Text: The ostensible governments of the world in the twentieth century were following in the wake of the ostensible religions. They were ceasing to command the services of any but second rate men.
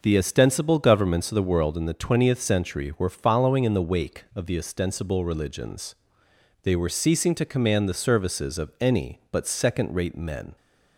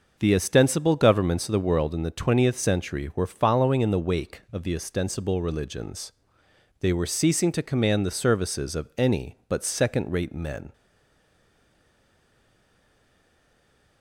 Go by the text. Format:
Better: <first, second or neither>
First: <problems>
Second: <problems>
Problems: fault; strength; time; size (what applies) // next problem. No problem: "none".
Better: first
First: none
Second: stays silent after the last word; strong; from 10.7 s on; 3.3 s long